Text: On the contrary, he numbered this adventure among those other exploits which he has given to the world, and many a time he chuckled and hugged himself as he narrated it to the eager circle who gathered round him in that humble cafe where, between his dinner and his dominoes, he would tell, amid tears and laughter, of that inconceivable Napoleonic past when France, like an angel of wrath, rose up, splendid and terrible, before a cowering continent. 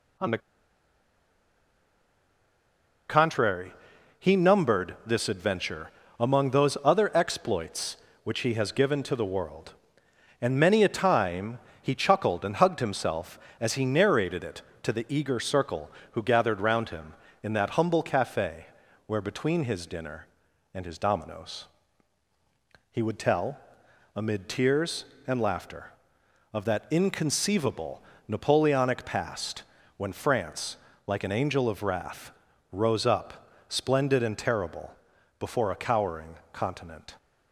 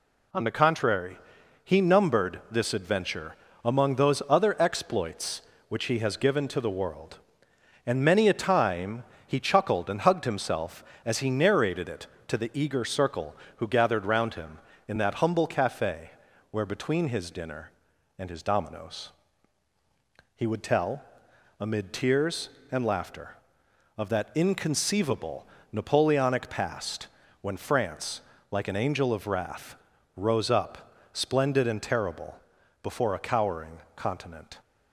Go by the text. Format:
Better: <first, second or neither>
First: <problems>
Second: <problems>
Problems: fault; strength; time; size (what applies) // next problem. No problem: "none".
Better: second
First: pauses between "the" and "contrary"; strong; at 0.3 s; 2.7 s long // pauses between "adventure" and "among"; slight; at 5.9 s; 0.30 s long // pauses between "time" and "he"; slight; at 11.5 s; 0.24 s long // pauses between "cafe" and "where"; at 18.6 s; 0.42 s long // pauses between "inconceivable" and "Napoleonic"; slight; at 28.0 s; 0.28 s long // pauses between "past" and "when"; slight; at 29.6 s; 0.32 s long // pauses between "cowering" and "continent"; slight; at 36.3 s; 0.18 s long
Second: pauses between "adventure" and "among"; slight; at 3.3 s; 0.30 s long // pauses between "time" and "he"; slight; at 9.0 s; 0.24 s long // pauses between "cafe" and "where"; at 16.1 s; 0.42 s long // pauses between "inconceivable" and "Napoleonic"; slight; at 25.4 s; 0.28 s long // pauses between "past" and "when"; slight; at 27.0 s; 0.32 s long // pauses between "cowering" and "continent"; slight; at 33.7 s; 0.18 s long